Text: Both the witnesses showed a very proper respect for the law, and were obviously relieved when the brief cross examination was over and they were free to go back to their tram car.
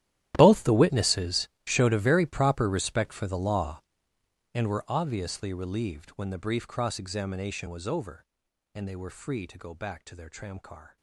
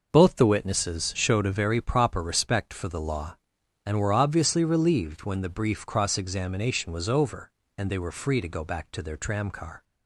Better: second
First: gets quieter; strong; throughout; 19 dB // pauses between "witnesses" and "showed"; slight; at 1.4 s; 0.18 s long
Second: none

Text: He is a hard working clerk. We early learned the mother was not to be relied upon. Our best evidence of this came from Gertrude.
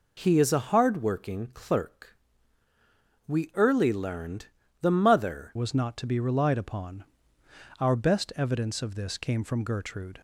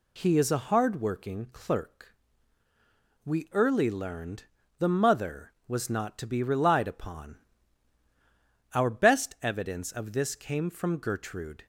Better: second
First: pauses between "learned" and "the"; slight; at 4.4 s; 0.36 s long // changes voice at "was"; from 5.5 s on; 4.7 s long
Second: pauses between "learned" and "the"; slight; at 4.4 s; 0.36 s long

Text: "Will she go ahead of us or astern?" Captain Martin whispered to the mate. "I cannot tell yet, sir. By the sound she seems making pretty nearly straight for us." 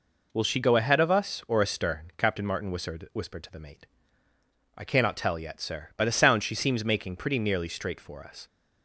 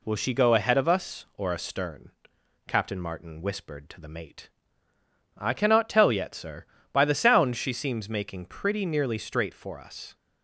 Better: second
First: says "whispered" twice; at 3.1 s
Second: none

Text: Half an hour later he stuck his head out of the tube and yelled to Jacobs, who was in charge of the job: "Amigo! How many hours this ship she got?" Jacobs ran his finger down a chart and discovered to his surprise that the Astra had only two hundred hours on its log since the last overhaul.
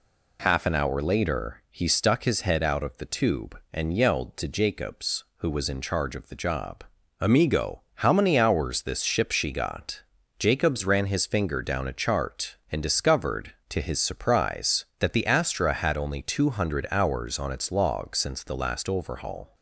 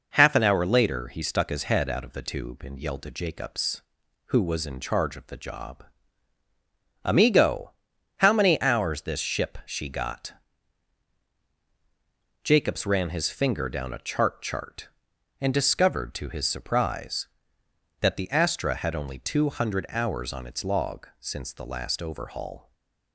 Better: first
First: none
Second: says "chart" twice; at 14.4 s // stays silent after the last word; slight; from 22.6 s on; 0.5 s long

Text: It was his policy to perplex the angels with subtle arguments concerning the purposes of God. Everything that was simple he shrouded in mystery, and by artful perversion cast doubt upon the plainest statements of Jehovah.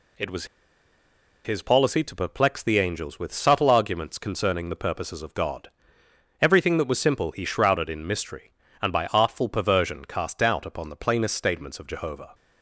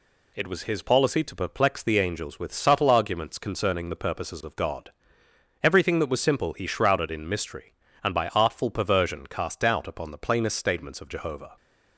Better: second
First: pauses between "was" and "his"; at 0.4 s; 0.99 s long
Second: none

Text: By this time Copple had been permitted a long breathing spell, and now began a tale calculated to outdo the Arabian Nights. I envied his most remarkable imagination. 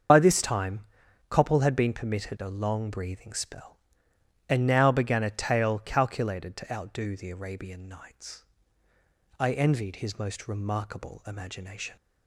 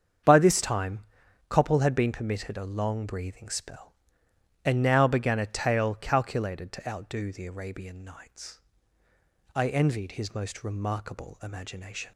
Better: second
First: loses the start of "By"; at 0.0 s; 40 ms // starts louder than the rest; strong; until 1.5 s; 7 dB // pauses between "time" and "Copple"; noticeable; at 0.7 s; 0.48 s long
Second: starts louder than the rest; strong; until 1.7 s; 7.5 dB // pauses between "time" and "Copple"; noticeable; at 0.9 s; 0.48 s long

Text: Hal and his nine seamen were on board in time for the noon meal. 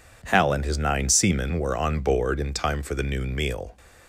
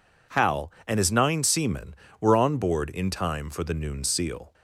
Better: first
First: none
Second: says "seal" for "meal"; at 4.0 s

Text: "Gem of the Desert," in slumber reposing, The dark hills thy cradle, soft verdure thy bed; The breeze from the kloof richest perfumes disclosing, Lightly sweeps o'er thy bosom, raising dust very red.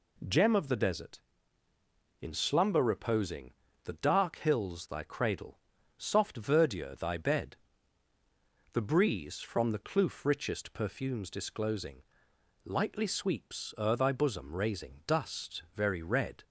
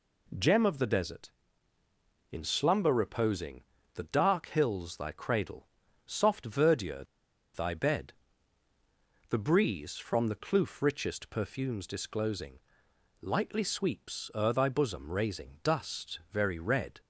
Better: first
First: none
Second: pauses between "verdure" and "thy"; noticeable; at 7.0 s; 0.50 s long

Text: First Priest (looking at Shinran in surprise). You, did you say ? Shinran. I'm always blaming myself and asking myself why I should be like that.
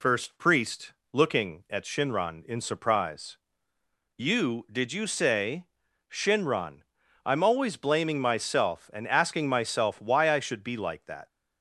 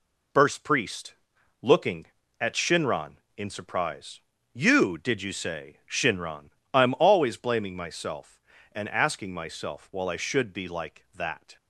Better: first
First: none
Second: says "while" for "why"; at 9.9 s

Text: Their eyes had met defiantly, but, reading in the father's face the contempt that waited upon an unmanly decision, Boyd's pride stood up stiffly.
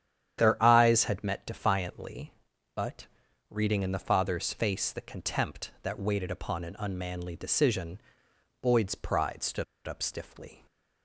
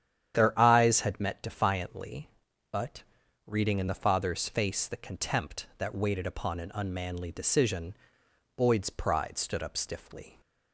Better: second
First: starts louder than the rest; strong; until 1.4 s; 9.5 dB // pauses between "stood" and "up"; slight; at 9.6 s; 0.22 s long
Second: starts louder than the rest; strong; until 1.4 s; 9.5 dB

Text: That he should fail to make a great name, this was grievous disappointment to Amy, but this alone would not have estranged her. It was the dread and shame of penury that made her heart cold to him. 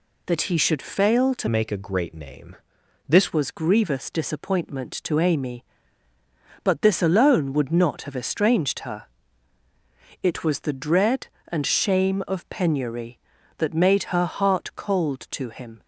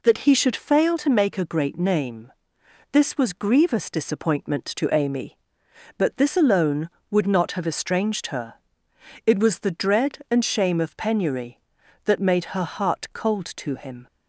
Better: second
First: changes voice from "make" to "this"; from 1.4 to 3.3 s; 1.9 s long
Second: none

